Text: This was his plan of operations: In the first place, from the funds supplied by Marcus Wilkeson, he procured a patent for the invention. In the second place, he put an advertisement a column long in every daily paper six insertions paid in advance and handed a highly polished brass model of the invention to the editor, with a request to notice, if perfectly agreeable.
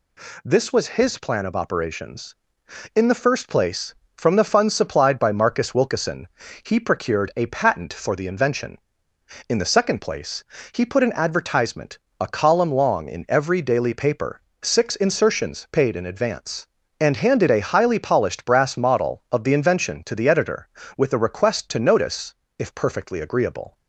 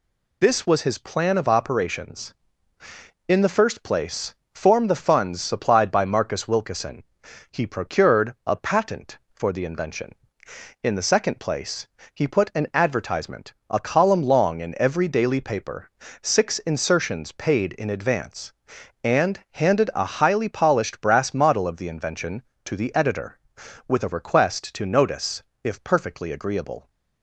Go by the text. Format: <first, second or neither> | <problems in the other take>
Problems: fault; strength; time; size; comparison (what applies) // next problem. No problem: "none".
first | says "form" for "from"; at 4.5 s // pauses between "advertisement" and "a"; slight; at 13.5 s; 0.16 s long; slight in the first // pauses between "paper" and "six"; slight; at 15.8 s; 0.36 s long; slight in the first